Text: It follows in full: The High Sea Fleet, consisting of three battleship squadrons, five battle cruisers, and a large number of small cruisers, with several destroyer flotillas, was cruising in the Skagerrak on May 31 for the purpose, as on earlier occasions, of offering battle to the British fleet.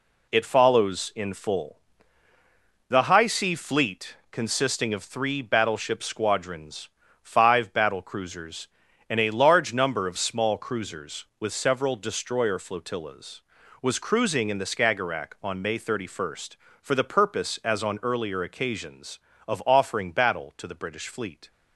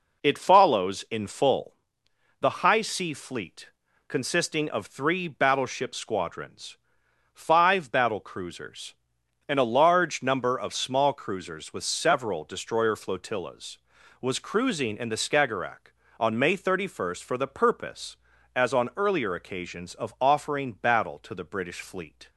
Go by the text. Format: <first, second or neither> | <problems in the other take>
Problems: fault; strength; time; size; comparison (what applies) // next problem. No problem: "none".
neither | none